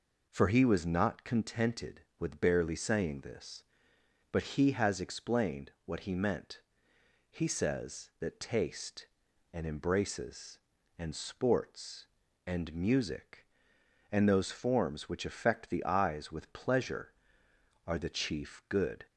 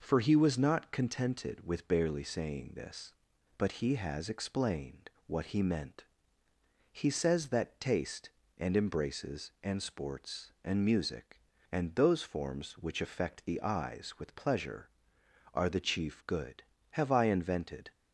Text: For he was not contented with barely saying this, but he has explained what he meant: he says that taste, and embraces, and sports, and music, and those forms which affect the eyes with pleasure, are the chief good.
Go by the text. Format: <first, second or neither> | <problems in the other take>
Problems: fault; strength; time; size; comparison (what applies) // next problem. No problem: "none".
first | pauses between "explained" and "what"; slight; at 5.0 s; 0.18 s long // goes on to say "Have I invented"; noticeable; from 16.9 s on; 0.98 s long